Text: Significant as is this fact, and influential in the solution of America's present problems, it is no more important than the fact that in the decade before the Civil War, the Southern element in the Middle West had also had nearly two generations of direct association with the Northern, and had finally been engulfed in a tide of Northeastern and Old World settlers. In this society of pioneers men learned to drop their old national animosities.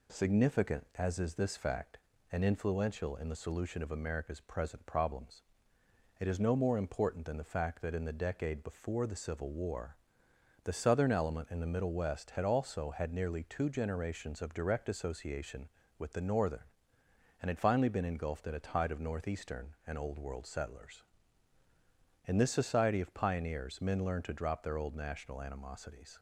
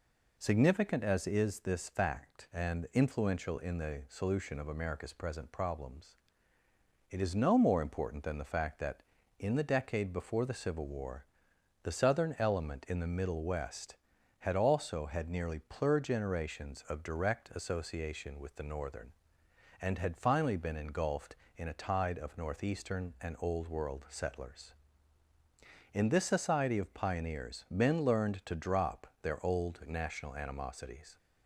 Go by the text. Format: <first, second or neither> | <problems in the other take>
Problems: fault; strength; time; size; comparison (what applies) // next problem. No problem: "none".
first | says "plur" for "two"; at 15.6 s // pauses between "drop" and "their"; slight; at 29.0 s; 0.16 s long